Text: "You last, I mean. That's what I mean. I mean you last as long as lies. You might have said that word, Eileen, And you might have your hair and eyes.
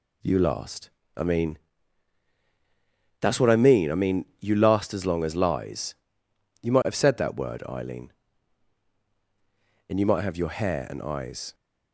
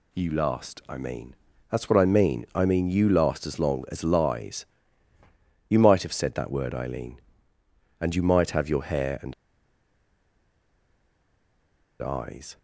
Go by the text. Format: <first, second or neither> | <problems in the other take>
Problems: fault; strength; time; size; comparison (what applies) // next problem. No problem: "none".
first | pauses between "and" and "eyes"; strong; at 9.3 s; 2.6 s long